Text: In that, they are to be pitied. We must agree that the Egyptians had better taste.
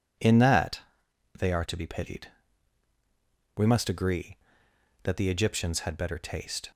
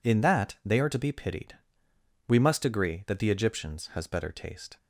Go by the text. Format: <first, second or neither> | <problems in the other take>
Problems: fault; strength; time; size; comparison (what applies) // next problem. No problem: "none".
first | says "has" for "had"; at 3.9 s